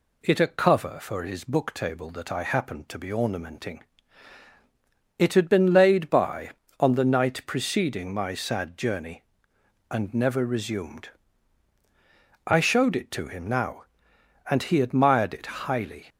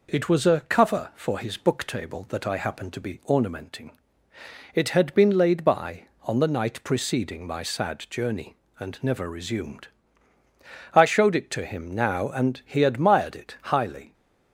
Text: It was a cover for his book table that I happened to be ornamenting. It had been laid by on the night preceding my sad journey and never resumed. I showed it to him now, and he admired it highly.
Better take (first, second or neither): second